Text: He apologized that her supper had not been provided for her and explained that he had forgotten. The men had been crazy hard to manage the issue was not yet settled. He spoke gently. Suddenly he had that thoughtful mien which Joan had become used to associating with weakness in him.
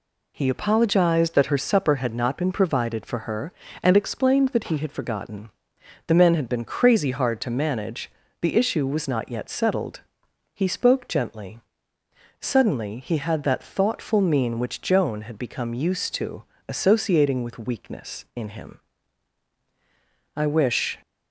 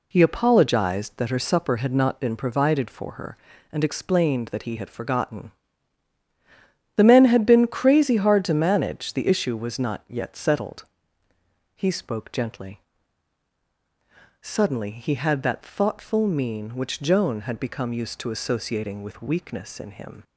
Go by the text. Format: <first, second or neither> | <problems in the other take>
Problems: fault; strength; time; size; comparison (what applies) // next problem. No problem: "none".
second | pauses between "manage" and "the"; slight; at 8.0 s; 0.30 s long // pauses between "to" and "associating"; slight; at 16.4 s; 0.22 s long // goes on to say "I wish"; noticeable; from 20.3 s on; 0.64 s long